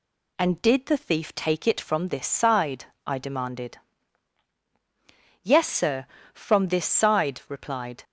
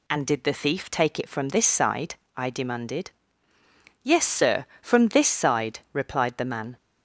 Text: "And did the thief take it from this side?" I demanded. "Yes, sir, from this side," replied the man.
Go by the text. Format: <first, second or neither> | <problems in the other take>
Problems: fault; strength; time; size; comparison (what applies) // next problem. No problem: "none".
second | stops before "the man"; at 8.0 s